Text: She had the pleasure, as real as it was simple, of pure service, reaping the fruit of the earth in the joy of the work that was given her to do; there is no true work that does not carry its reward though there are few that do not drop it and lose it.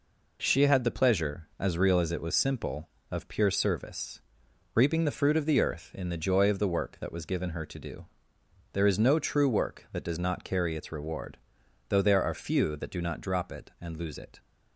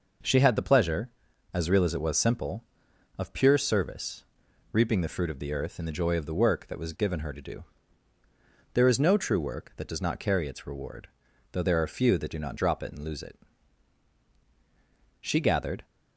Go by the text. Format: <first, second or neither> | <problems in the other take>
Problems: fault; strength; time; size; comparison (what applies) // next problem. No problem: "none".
first | pauses between "reward" and "though"; at 11.0 s; 0.44 s long; noticeable in the first // goes on to say "She gathered"; noticeable; from 15.2 s on; 0.64 s long